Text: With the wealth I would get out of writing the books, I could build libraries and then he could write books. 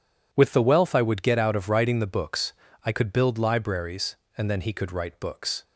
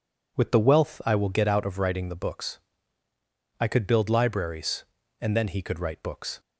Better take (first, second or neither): first